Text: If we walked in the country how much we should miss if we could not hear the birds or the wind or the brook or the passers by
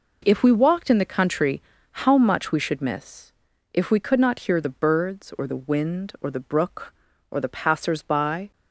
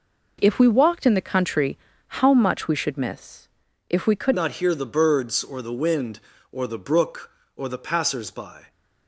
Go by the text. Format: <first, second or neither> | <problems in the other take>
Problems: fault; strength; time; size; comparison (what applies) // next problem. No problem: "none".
first | pauses between "country" and "how"; at 1.7 s; 0.42 s long; also in the first // pauses between "miss" and "if"; at 3.4 s; 0.40 s long; also in the first // changes voice at "not"; from 4.3 s on; 4.3 s long